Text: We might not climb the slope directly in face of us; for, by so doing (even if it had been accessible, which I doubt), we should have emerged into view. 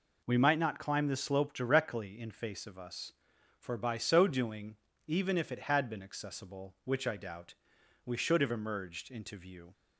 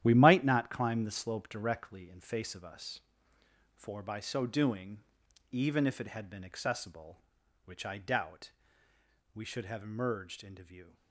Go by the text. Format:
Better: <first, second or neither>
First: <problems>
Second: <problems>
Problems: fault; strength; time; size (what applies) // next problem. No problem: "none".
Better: first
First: none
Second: gets quieter; strong; throughout; 10.5 dB